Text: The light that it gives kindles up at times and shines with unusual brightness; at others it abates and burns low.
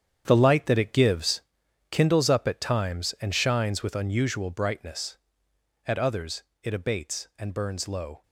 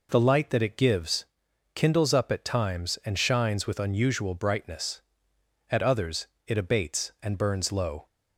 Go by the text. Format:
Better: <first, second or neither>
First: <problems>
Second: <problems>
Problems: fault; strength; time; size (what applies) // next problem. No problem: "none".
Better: second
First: gets quieter; strong; throughout; 12.5 dB // pauses between "gives" and "kindles"; noticeable; at 1.4 s; 0.52 s long // pauses between "others" and "it"; slight; at 6.4 s; 0.22 s long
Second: pauses between "gives" and "kindles"; noticeable; at 1.2 s; 0.52 s long // pauses between "others" and "it"; slight; at 6.2 s; 0.22 s long